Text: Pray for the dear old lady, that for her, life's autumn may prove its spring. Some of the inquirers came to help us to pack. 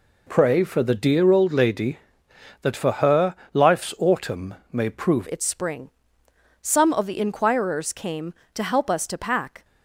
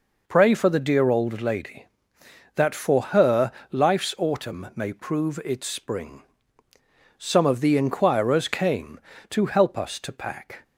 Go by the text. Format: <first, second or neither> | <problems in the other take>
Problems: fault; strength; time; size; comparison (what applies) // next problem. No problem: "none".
second | pauses between "autumn" and "may"; slight; at 4.5 s; 0.16 s long // changes voice at "its"; from 5.3 s on; 4.3 s long